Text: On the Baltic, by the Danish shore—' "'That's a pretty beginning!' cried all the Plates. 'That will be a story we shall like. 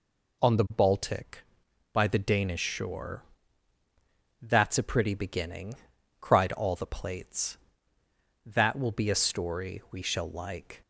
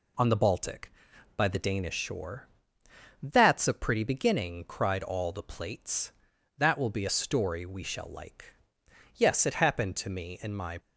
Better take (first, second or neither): first